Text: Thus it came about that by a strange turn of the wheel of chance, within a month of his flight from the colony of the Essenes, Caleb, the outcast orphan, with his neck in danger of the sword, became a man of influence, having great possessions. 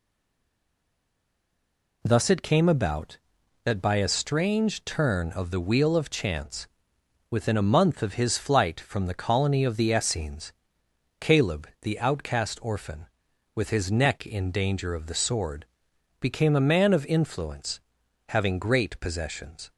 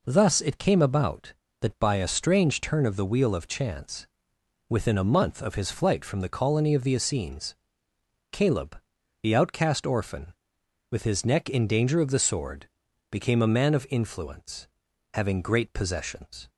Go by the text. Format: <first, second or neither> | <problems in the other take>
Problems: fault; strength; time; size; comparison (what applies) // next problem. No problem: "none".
second | stays silent before the first word; noticeable; until 2.0 s; 2.0 s long